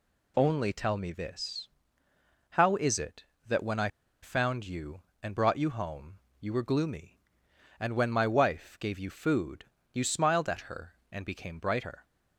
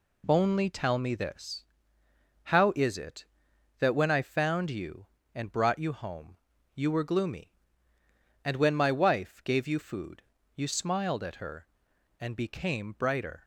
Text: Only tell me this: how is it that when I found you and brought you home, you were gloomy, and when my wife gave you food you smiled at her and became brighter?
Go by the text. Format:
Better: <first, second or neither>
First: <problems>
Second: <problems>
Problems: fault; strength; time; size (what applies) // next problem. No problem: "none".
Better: second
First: pauses between "I" and "found"; slight; at 3.8 s; 0.35 s long // pauses between "food" and "you"; slight; at 9.6 s; 0.30 s long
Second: pauses between "food" and "you"; slight; at 10.2 s; 0.34 s long